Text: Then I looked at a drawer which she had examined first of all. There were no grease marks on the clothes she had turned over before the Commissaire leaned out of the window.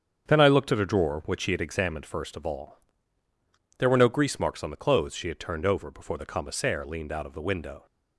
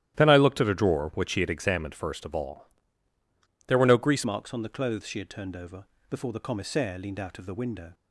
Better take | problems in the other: first | starts louder than the rest; strong; until 1.1 s; 12.5 dB; strong in the first // changes voice at "marks"; from 4.2 s on; 3.7 s long // pauses between "over" and "before"; slight; at 5.8 s; 0.24 s long

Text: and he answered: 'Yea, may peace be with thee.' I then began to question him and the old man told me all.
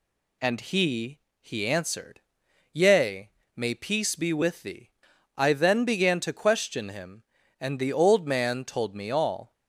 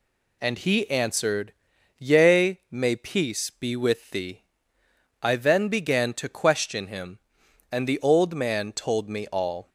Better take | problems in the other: second | says "he" twice; at 1.4 s

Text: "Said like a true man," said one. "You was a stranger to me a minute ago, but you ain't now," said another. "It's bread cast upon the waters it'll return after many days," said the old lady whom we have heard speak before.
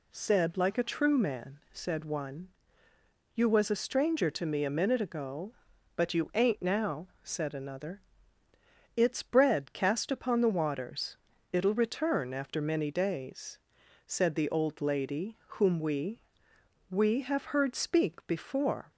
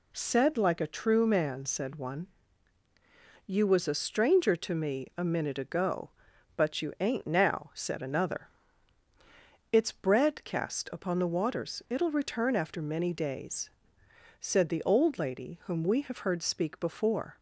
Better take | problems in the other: second | pauses between "waters" and "it'll"; slight; at 11.1 s; 0.36 s long // says "we" twice; at 16.9 s

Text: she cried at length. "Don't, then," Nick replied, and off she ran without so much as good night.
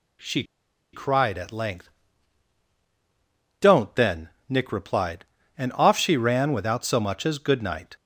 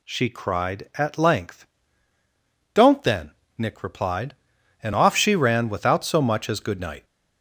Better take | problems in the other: second | pauses between "she" and "cried"; noticeable; at 0.4 s; 0.49 s long

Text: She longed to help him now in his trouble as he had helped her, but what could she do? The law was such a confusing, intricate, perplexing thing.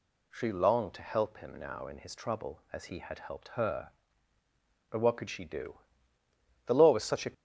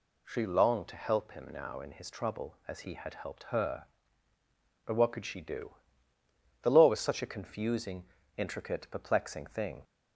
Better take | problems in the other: second | stops before "confusing intricate perplexing thing"; at 7.3 s

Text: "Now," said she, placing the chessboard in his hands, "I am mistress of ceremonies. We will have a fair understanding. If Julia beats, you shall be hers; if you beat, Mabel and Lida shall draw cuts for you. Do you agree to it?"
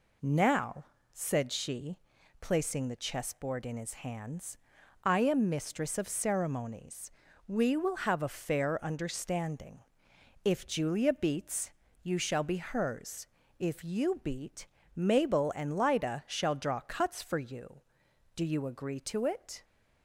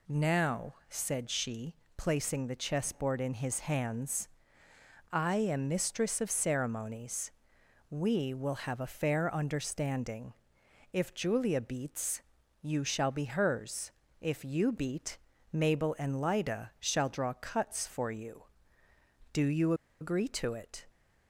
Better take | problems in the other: first | pauses between "you" and "agree"; slight; at 19.7 s; 0.27 s long

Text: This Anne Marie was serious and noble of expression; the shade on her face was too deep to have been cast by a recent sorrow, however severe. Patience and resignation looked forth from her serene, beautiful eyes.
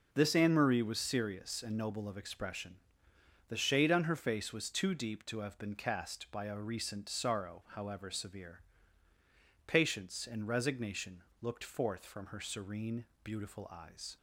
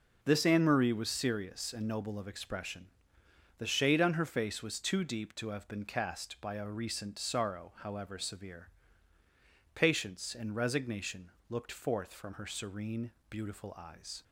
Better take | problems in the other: neither | pauses between "resignation" and "looked"; slight; the same in both

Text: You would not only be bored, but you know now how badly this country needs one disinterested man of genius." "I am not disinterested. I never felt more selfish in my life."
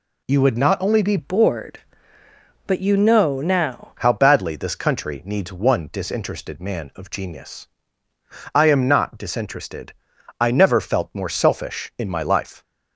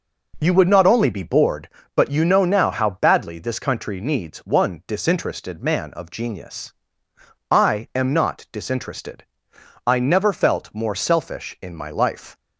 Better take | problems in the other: second | changes voice from "bored" to "now"; from 1.1 to 3.9 s; 2.8 s long

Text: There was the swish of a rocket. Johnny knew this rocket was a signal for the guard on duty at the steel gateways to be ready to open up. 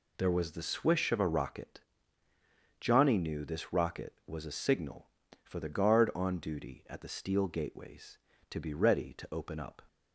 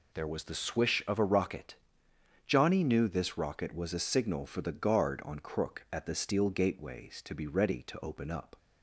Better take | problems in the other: first | says "crook" for "duty"; at 5.3 s

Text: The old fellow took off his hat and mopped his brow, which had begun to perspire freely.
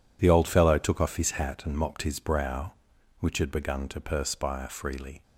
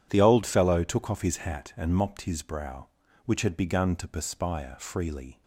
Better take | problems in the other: neither | none

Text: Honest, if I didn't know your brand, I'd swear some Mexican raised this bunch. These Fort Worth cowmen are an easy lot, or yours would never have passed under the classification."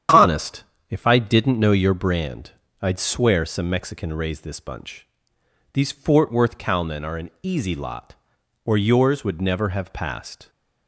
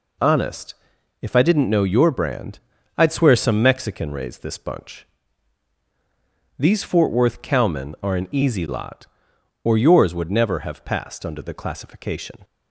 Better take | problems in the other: second | starts louder than the rest; strong; until 1.3 s; 9.5 dB // stops before "under the classification"; at 10.4 s

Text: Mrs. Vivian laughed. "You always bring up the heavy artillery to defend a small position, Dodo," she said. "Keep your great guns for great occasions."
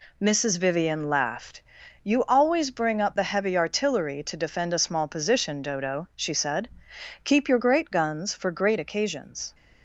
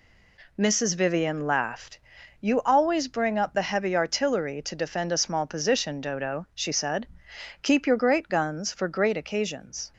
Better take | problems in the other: neither | none

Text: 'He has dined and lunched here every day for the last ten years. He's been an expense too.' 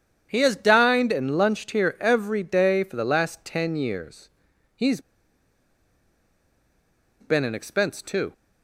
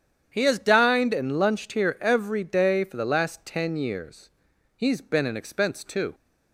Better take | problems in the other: second | starts louder than the rest; strong; until 1.3 s; 9 dB; strong in the second // pauses between "He's" and "been"; strong; at 4.9 s; 2.2 s long

